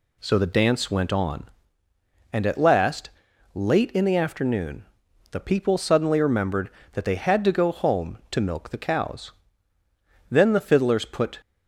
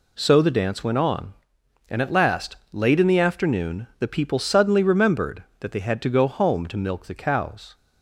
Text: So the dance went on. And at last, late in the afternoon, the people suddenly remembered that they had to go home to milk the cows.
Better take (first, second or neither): second